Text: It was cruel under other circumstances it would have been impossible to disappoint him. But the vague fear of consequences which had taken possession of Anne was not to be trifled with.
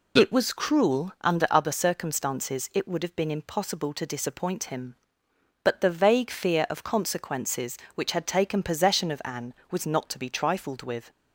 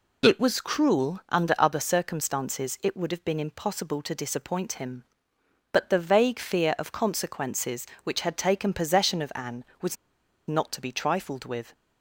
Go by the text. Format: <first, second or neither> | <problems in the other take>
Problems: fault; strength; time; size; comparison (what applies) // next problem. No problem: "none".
first | pauses between "was" and "not"; noticeable; at 9.9 s; 0.54 s long